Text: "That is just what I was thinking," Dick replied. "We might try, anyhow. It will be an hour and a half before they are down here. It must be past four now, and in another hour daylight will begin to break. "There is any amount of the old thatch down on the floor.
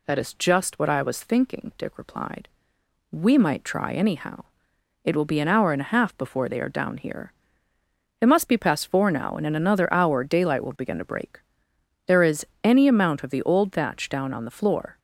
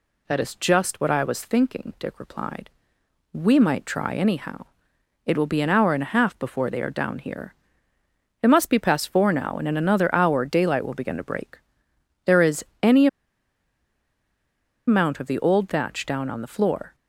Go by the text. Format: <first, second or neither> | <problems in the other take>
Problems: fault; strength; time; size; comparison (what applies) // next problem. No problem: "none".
first | pauses between "is" and "any"; slight; at 12.6 s; 0.16 s long; slight in the first // pauses between "any" and "amount"; strong; at 13.0 s; 1.8 s long